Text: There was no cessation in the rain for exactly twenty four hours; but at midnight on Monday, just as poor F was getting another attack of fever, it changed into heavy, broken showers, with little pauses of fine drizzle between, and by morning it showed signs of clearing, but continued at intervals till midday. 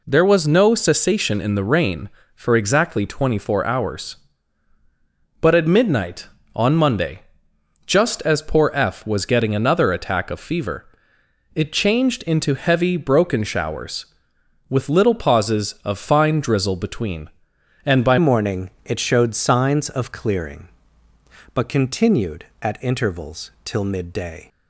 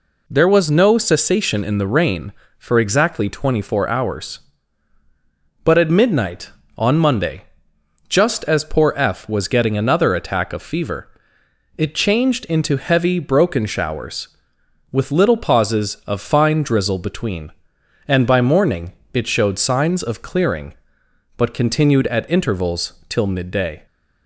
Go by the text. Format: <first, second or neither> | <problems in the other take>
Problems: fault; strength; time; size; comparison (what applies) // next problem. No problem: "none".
second | changes voice at "morning"; from 18.1 s on; 6.3 s long // pauses between "morning" and "it"; slight; at 18.7 s; 0.16 s long; slight in the second // pauses between "intervals" and "till"; slight; at 23.5 s; 0.16 s long; slight in the second